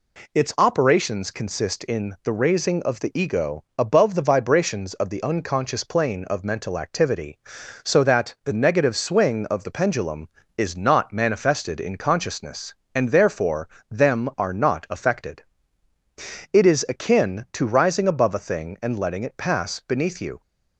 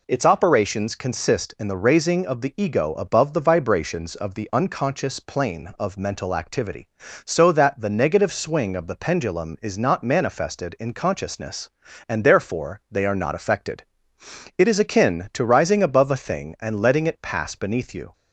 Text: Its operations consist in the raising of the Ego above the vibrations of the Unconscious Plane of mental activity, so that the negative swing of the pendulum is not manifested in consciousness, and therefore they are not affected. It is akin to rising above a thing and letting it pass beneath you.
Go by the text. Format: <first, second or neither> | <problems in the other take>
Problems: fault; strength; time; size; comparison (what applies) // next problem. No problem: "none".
second | says "them" for "they"; at 13.9 s